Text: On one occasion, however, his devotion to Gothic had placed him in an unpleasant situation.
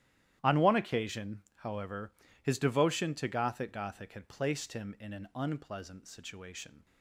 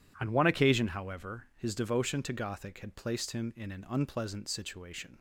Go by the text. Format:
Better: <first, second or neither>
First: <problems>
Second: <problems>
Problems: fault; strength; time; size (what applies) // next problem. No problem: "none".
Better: second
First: starts louder than the rest; strong; until 1.4 s; 12 dB // says "Gothic" twice; at 3.7 s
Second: none